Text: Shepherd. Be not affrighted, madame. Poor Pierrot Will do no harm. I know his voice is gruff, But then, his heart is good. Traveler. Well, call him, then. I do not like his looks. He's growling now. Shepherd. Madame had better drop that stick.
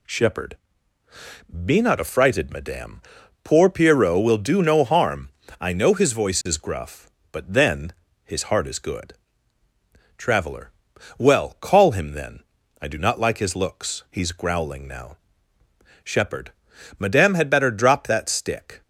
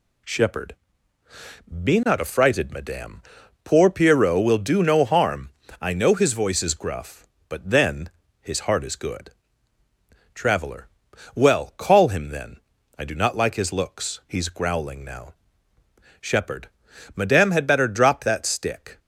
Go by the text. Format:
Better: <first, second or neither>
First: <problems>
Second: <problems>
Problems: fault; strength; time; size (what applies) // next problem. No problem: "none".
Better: neither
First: none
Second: none